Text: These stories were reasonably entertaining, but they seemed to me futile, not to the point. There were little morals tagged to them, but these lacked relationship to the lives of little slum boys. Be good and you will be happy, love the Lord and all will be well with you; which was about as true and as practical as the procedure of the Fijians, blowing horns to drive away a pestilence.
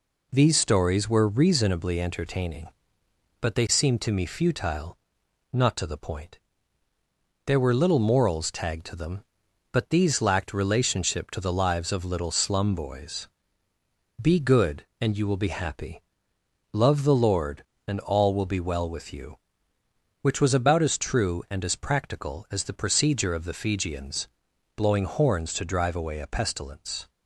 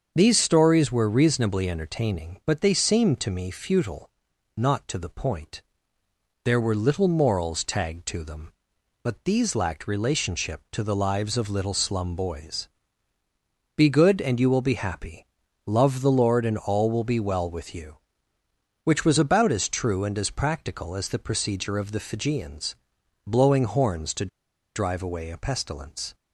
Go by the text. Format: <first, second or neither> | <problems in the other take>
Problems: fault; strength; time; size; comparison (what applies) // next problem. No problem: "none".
first | starts louder than the rest; until 1.1 s; 7 dB // pauses between "to" and "drive"; noticeable; at 24.2 s; 0.48 s long